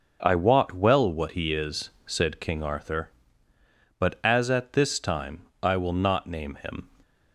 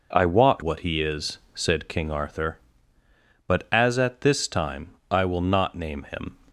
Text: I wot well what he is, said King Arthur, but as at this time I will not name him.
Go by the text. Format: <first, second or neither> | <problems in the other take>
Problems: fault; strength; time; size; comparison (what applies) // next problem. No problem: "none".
first | skips "well"; at 0.6 s // pauses between "time" and "I"; slight; at 4.9 s; 0.16 s long; slight in the first